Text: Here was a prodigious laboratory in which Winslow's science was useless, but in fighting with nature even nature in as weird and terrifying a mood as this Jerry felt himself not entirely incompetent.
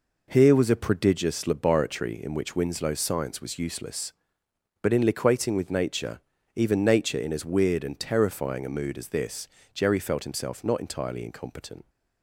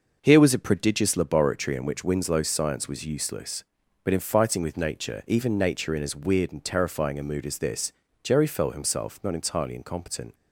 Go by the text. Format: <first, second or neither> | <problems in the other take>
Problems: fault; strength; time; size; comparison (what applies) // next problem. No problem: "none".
second | says "liquating" for "fighting"; at 5.0 s // pauses between "nature" and "even"; slight; at 6.2 s; 0.34 s long // pauses between "this" and "Jerry"; slight; at 9.4 s; 0.26 s long; slight in the second